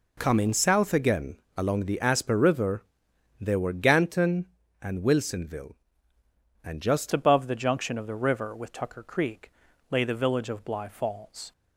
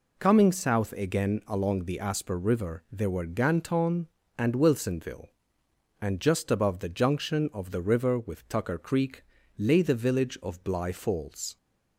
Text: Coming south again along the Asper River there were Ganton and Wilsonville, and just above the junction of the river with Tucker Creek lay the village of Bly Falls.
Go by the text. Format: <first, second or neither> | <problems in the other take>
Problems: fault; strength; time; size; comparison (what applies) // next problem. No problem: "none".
second | pauses between "again" and "along"; slight; at 1.3 s; 0.18 s long // pauses between "River" and "there"; noticeable; at 2.8 s; 0.58 s long // changes voice at "above"; from 7.1 s on; 4.4 s long // pauses between "Creek" and "lay"; at 9.5 s; 0.38 s long; slight in the second